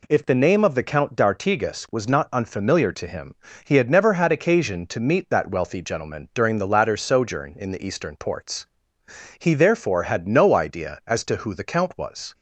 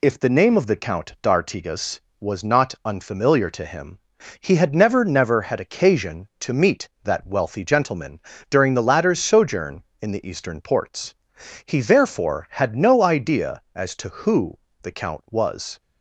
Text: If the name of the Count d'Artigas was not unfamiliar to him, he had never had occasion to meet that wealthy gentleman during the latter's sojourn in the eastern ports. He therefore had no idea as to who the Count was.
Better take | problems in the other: first | says "never" twice; at 5.0 s // pauses between "gentleman" and "during"; slight; at 8.1 s; 0.30 s long // pauses between "who" and "the"; slight; at 14.5 s; 0.28 s long

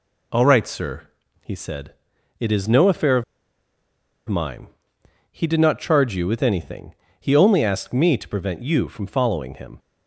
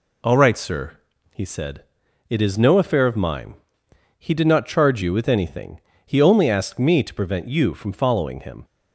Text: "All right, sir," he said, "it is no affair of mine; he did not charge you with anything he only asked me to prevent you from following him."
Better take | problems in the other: second | pauses between "of" and "mine"; at 3.2 s; 1.0 s long // pauses between "anything" and "he"; slight; at 6.9 s; 0.26 s long; slight in the second

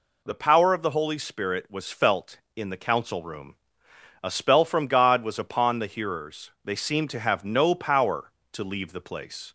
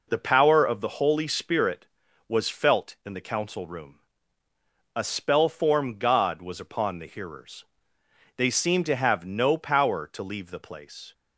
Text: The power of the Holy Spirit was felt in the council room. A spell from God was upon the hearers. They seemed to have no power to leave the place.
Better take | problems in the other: first | says "form" for "from"; at 5.4 s

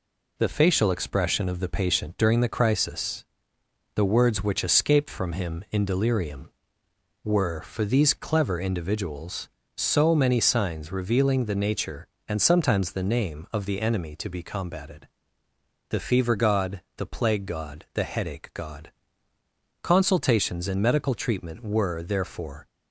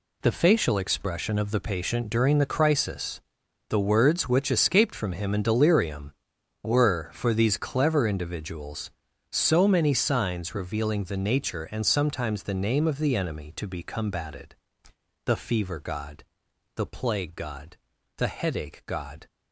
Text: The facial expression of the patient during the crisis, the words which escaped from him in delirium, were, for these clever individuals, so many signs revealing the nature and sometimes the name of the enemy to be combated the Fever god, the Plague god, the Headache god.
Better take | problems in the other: second | pauses between "combated" and "the"; noticeable; at 15.0 s; 0.84 s long; noticeable in the second // goes on to say "Consultations and medical treatment were therefore"; strong; from 19.8 s on; 2.8 s long

